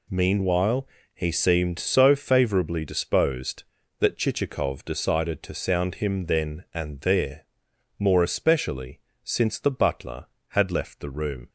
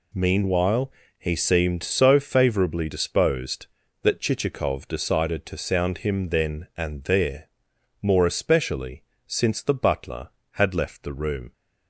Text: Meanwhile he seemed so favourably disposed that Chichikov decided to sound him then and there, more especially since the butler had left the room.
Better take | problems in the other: neither | pauses between "Meanwhile" and "he"; slight; the same in both // pauses between "especially" and "since"; slight; the same in both

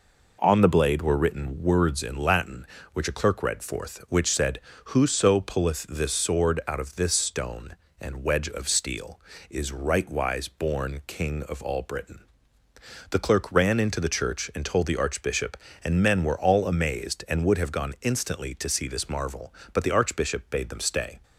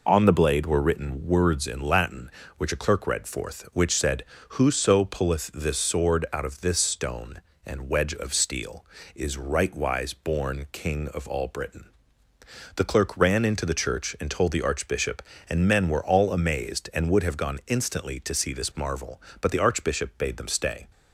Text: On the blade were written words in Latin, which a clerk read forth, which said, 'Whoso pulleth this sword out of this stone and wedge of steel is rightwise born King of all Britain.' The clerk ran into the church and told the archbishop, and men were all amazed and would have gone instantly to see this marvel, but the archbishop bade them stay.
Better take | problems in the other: first | loses the start of "On"; at 0.0 s; 35 ms

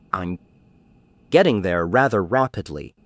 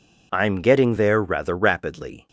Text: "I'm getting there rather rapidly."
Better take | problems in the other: second | pauses between "I'm" and "getting"; noticeable; at 0.3 s; 0.95 s long

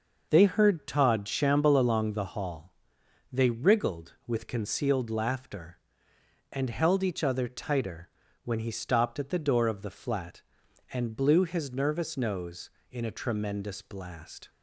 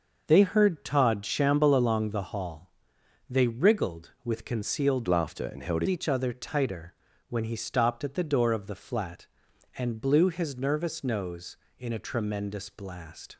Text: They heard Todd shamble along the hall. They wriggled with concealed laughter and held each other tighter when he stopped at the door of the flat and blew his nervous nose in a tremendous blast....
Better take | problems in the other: first | starts louder than the rest; noticeable; until 1.2 s; 6 dB // changes voice from "laughter" to "held"; from 5.0 to 5.8 s; 0.8 s long // pauses between "tighter" and "when"; slight; at 6.9 s; 0.36 s long; slight in the first

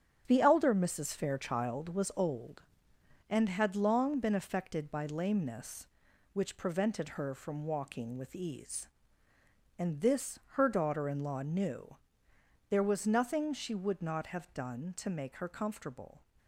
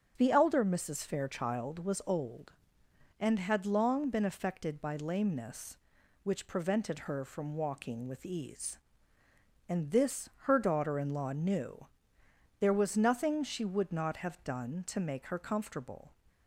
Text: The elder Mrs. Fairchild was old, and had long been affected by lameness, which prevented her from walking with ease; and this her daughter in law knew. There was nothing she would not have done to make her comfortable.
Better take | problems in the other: second | gets quieter; strong; throughout; 7.5 dB // starts louder than the rest; strong; until 1.2 s; 9.5 dB; strong in the second

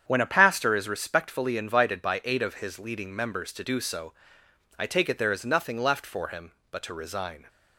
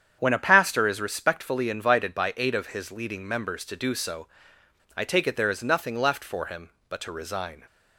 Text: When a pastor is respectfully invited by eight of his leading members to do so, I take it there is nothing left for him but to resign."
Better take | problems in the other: neither | starts louder than the rest; strong; the same in both

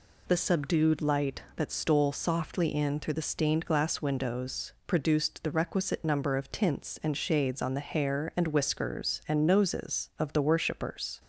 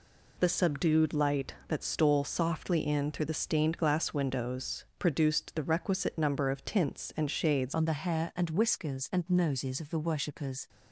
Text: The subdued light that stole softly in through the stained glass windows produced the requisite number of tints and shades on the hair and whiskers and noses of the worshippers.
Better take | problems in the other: first | pauses between "windows" and "produced"; slight; at 4.8 s; 0.16 s long; slight in the first // changes voice at "on"; from 7.7 s on; 2.9 s long

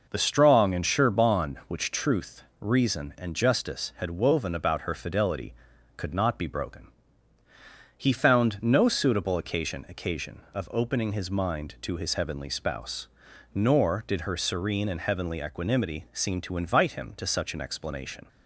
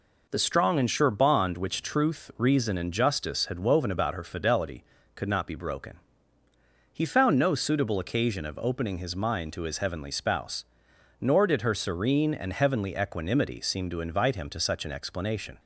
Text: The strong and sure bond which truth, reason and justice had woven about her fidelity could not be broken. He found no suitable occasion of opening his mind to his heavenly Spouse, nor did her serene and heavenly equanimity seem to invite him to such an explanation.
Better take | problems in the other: second | says "occasion" twice; at 9.8 s

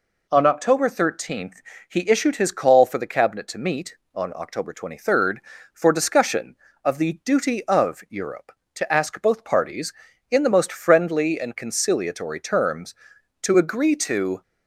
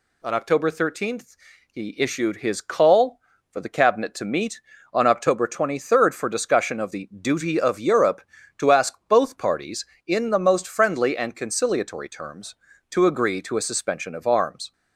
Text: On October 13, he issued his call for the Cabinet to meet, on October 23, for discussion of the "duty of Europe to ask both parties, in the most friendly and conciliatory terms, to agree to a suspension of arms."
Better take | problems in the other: second | stops before "a suspension of arms"; at 14.4 s

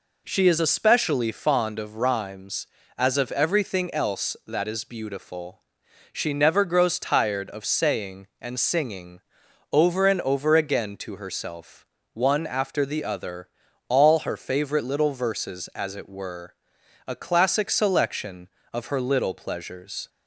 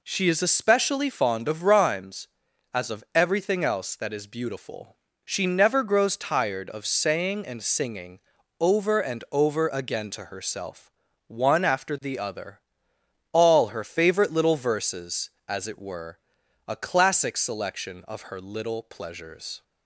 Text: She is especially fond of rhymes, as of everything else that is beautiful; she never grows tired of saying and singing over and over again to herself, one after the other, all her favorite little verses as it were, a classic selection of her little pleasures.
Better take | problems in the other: neither | pauses between "singing" and "over"; the same in both

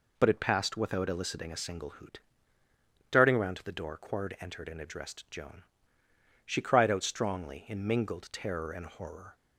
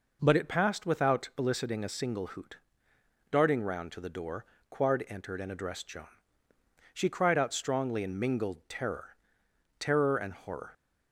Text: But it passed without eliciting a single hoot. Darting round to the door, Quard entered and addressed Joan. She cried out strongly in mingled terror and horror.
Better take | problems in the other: first | says "terror" twice; at 9.7 s

